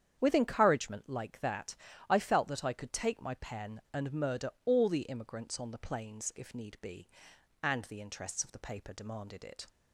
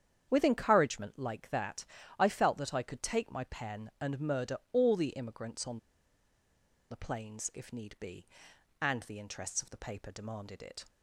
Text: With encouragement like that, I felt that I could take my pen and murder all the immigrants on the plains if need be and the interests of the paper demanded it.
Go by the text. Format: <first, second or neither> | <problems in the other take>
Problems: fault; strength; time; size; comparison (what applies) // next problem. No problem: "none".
first | starts louder than the rest; strong; until 1.3 s; 8.5 dB; strong in the first // pauses between "murder" and "all"; slight; at 4.5 s; 0.16 s long; slight in the first // pauses between "on" and "the"; at 5.7 s; 1.1 s long